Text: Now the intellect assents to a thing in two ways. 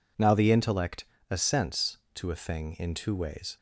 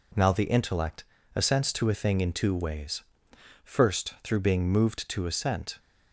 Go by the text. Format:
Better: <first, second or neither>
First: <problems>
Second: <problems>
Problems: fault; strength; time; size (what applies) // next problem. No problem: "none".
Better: first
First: pauses between "intellect" and "assents"; slight; at 1.0 s; 0.24 s long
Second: pauses between "intellect" and "assents"; slight; at 1.0 s; 0.30 s long // goes on to say "First through being moved to assent"; strong; from 3.6 s on; 2.1 s long